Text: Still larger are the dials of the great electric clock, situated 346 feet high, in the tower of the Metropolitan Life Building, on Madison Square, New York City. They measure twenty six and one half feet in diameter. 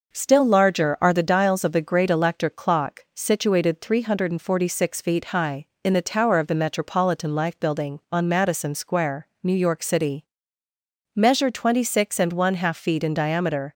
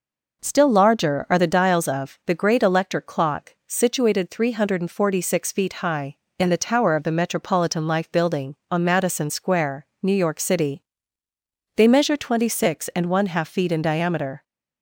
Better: second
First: skips "They"; at 10.6 s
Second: none

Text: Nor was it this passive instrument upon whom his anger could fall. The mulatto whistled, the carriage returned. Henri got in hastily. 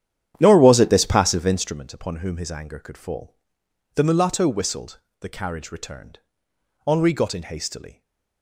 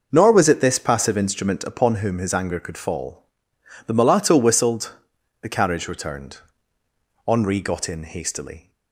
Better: second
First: starts louder than the rest; strong; until 1.8 s; 10 dB // stays silent after the last word; slight; from 7.9 s on; 0.5 s long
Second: none

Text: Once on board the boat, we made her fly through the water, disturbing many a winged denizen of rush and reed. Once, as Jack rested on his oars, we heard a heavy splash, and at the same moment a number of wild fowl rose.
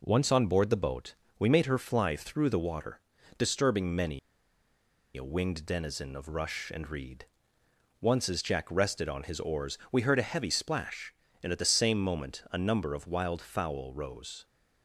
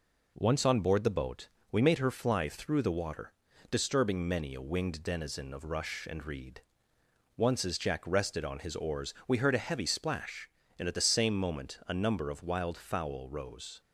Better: second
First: pauses between "many" and "a"; noticeable; at 4.1 s; 0.97 s long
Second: none

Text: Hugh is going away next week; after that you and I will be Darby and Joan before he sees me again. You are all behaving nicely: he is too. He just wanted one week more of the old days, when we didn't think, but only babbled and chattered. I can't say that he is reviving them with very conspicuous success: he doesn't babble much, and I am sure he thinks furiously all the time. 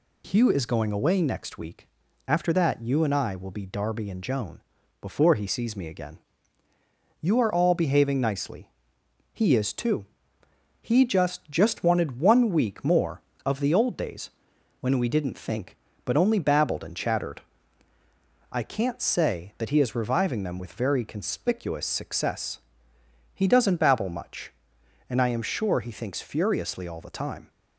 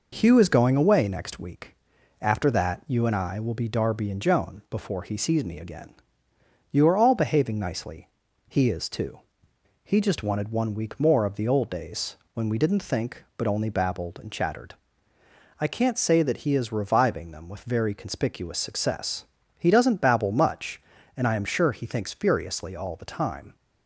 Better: second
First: pauses between "Joan" and "before"; at 4.5 s; 0.40 s long // says "just" twice; at 11.4 s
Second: none

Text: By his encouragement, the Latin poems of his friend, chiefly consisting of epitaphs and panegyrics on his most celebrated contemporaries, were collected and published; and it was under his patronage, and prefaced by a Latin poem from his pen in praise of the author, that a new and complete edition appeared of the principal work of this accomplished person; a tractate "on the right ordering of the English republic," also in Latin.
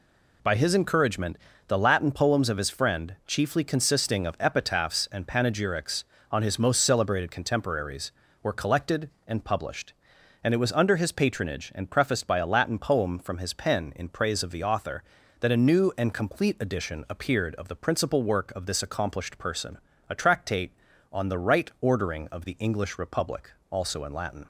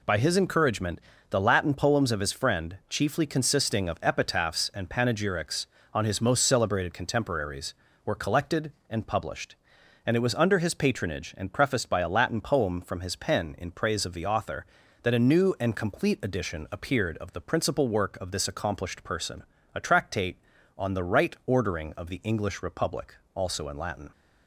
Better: neither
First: none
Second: none

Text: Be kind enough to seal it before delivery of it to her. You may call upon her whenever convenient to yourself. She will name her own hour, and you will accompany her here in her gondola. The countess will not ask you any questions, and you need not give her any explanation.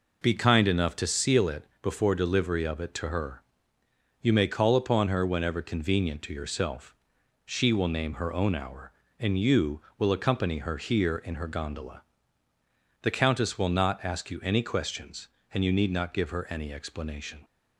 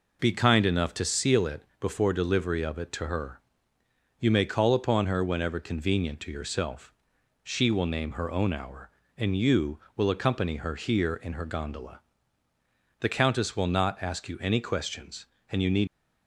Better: first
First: pauses between "it" and "before"; slight; at 1.6 s; 0.18 s long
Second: pauses between "it" and "before"; slight; at 1.6 s; 0.18 s long // stops before "not give her any explanation"; at 15.8 s

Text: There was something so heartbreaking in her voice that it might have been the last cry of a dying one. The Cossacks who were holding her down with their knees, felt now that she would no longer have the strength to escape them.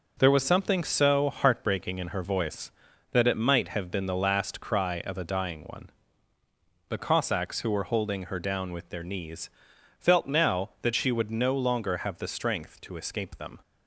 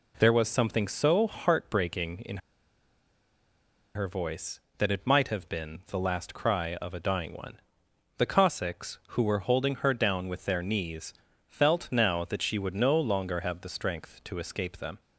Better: first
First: none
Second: pauses between "in" and "her"; strong; at 2.3 s; 1.5 s long

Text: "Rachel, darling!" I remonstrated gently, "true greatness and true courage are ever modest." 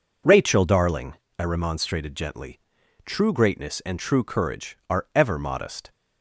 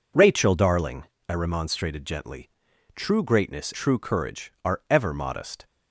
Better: first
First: none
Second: skips "and"; at 3.7 s

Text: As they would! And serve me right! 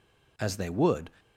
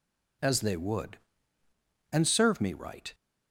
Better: second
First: stops before "And serve me right"; at 1.1 s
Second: none

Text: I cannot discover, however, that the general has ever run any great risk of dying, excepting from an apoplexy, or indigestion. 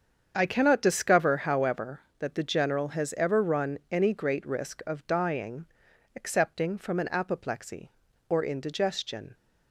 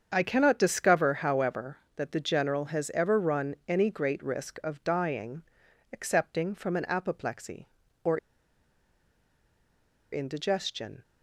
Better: first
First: starts louder than the rest; strong; until 1.3 s; 7.5 dB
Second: starts louder than the rest; strong; until 1.1 s; 7.5 dB // pauses between "or" and "indigestion"; strong; at 8.1 s; 1.9 s long

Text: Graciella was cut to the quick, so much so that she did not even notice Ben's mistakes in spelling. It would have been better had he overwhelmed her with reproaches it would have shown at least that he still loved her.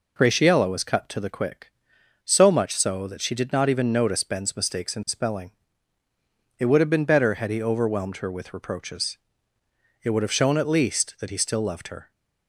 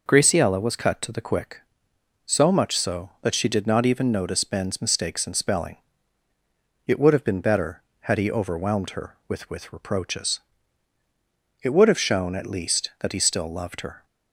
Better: first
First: pauses between "reproaches" and "it"; noticeable; at 9.1 s; 0.86 s long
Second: says "with" twice; at 9.5 s // pauses between "reproaches" and "it"; at 10.4 s; 1.2 s long

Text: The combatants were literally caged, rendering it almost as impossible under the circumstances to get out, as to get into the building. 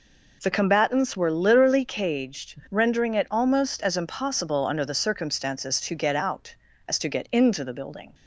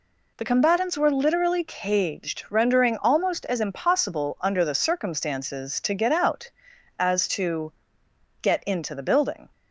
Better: first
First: none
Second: skips "it"; at 2.9 s // pauses between "to" and "get"; noticeable; at 7.7 s; 0.70 s long

